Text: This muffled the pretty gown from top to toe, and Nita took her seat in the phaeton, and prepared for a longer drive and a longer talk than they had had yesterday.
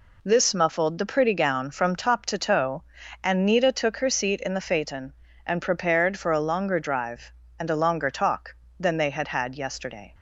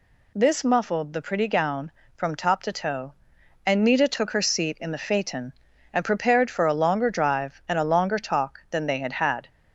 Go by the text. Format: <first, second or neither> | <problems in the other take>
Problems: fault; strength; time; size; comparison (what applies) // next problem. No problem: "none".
first | stops before "yesterday"; at 9.4 s